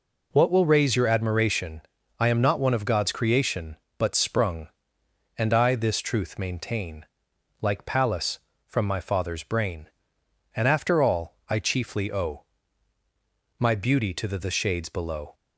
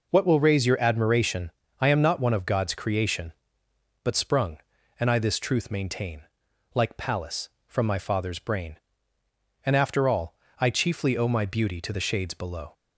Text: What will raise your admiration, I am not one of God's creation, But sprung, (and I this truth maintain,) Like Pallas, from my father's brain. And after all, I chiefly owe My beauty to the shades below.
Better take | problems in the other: second | pauses between "owe" and "My"; at 12.4 s; 1.1 s long // says "the" twice; at 14.3 s

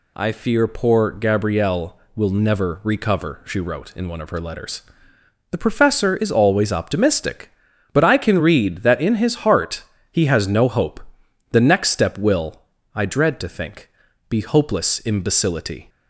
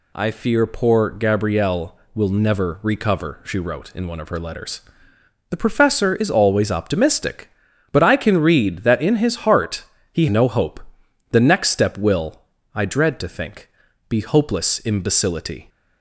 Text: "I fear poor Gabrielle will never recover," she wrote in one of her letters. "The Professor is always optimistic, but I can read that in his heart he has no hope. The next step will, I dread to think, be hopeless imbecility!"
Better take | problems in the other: first | pauses between "heart" and "he"; slight; at 9.8 s; 0.28 s long; slight in the first // skips "has"; at 10.2 s

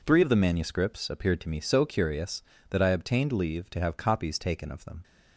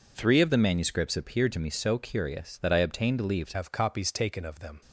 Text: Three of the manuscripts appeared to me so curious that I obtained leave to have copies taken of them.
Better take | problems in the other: first | changes voice at "have"; from 3.5 s on; 1.3 s long

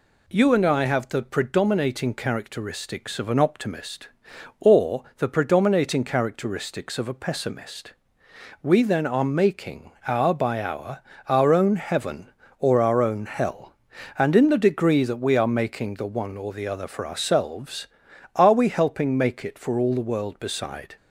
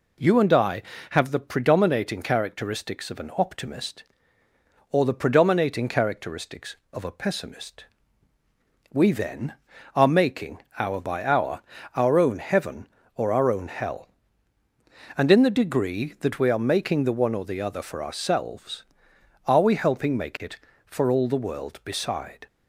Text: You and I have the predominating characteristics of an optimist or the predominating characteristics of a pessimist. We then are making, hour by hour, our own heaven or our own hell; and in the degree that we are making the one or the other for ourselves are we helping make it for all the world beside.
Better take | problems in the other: neither | none

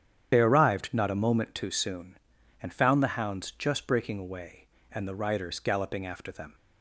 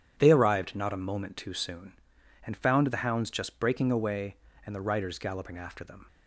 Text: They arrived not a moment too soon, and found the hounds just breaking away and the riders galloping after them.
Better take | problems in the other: second | loses the start of "They"; at 0.3 s; 40 ms // starts louder than the rest; strong; until 1.3 s; 9 dB; strong in the second

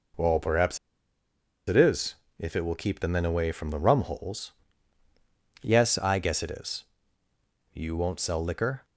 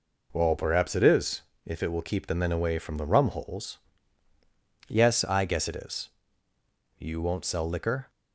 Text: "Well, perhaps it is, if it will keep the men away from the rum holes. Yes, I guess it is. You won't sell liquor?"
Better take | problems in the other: second | pauses between "perhaps" and "it"; noticeable; at 0.7 s; 0.90 s long

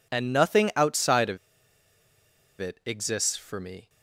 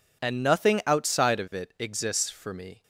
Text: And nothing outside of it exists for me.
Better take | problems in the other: second | pauses between "of" and "it"; at 1.3 s; 1.2 s long

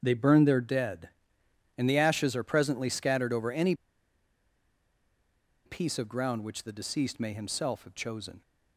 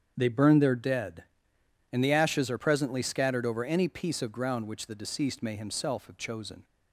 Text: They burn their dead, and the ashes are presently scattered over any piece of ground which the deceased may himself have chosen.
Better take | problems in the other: second | starts louder than the rest; strong; until 1.0 s; 8 dB; strong in the second // pauses between "any" and "piece"; strong; at 3.7 s; 1.9 s long

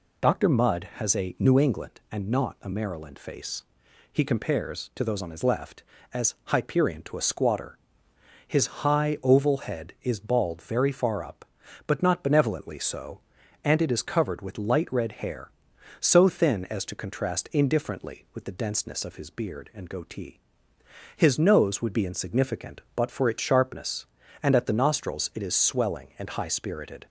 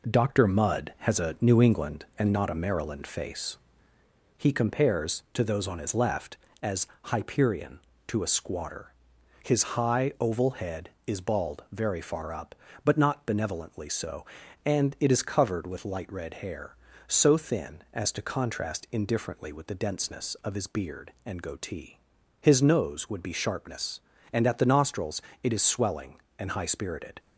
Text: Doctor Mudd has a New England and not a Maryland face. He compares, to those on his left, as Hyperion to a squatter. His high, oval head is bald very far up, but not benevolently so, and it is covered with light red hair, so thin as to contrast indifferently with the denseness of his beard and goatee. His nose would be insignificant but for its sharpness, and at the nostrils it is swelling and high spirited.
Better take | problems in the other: first | pauses between "as" and "Hyperion"; slight; at 6.8 s; 0.20 s long // skips "insignificant but for its"; at 23.3 s // pauses between "nostrils" and "it"; slight; at 25.2 s; 0.22 s long

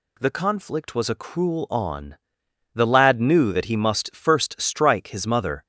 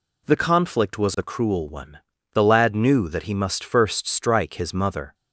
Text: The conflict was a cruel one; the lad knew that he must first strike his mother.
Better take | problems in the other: second | says "on" for "one"; at 1.6 s

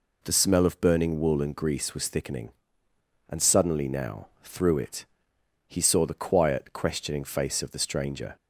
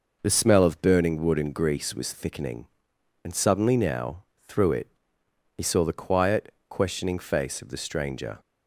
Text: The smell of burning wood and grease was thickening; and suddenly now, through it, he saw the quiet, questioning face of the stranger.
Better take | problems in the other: second | says "wool" for "wood"; at 1.1 s

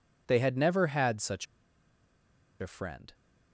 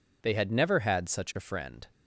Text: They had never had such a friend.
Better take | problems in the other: second | pauses between "such" and "a"; at 1.4 s; 1.1 s long

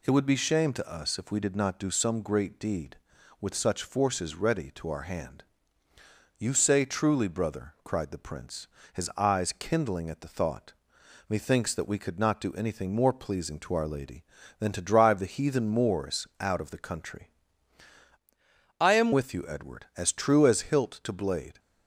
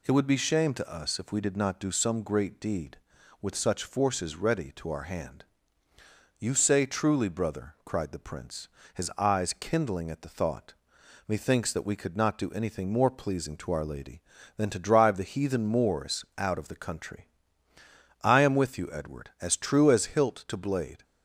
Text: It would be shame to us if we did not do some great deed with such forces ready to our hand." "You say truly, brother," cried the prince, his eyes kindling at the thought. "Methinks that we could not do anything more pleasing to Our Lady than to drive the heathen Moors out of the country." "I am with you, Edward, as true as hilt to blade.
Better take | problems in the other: second | changes voice from "I" to "am"; from 18.7 to 19.1 s; 0.4 s long

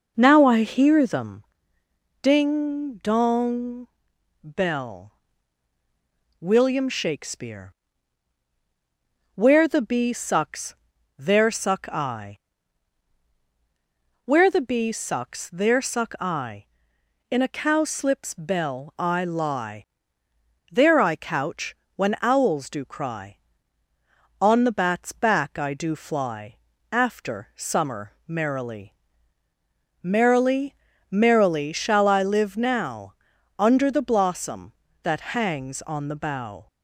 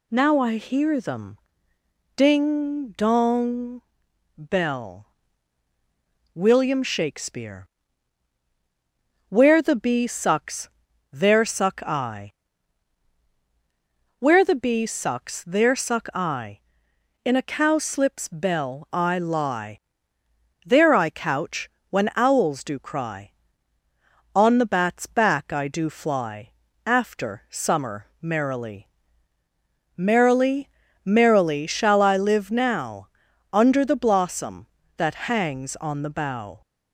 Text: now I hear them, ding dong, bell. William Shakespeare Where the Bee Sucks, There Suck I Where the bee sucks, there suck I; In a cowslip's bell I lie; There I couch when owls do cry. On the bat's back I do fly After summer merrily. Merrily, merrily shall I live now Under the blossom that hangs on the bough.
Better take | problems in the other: second | starts louder than the rest; noticeable; until 1.3 s; 5 dB // pauses between "Shakespeare" and "Where"; strong; at 7.7 s; 1.6 s long; strong in the second // pauses between "I" and "Where"; strong; at 12.3 s; 1.8 s long; strong in the second // pauses between "couch" and "when"; slight; at 21.7 s; 0.20 s long; slight in the second // pauses between "fly" and "After"; slight; at 26.5 s; 0.34 s long; slight in the second // pauses between "now" and "Under"; noticeable; at 33.1 s; 0.46 s long; noticeable in the second

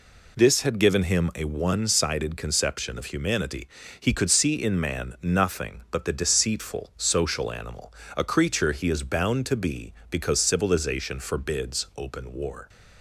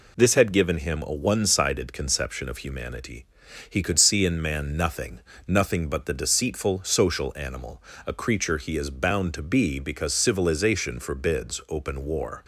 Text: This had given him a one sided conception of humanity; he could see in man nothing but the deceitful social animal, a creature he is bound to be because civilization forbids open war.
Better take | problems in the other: first | says "nothing" twice; at 5.4 s

